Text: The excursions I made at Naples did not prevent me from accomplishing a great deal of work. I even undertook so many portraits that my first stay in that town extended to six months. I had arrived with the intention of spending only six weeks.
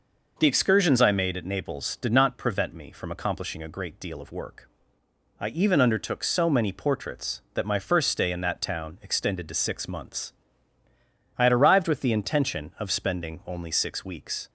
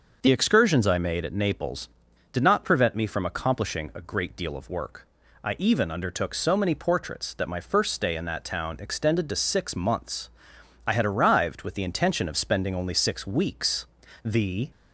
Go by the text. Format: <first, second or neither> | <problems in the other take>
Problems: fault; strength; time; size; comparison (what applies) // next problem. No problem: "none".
first | starts louder than the rest; noticeable; until 1.2 s; 6 dB // goes on to say "The"; slight; from 14.2 s on; 0.46 s long